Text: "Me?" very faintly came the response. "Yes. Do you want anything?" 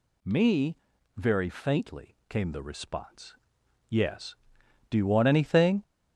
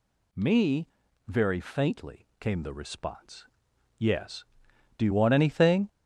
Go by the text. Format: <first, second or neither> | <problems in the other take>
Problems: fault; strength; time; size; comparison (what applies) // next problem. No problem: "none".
neither | none